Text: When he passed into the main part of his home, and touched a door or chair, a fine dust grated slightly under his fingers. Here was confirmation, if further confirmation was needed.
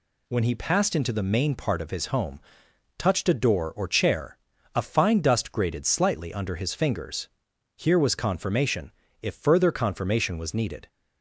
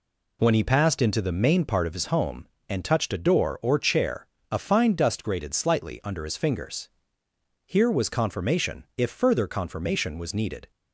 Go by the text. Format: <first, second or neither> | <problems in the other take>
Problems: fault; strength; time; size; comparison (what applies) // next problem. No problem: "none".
second | skips "and"; at 2.6 s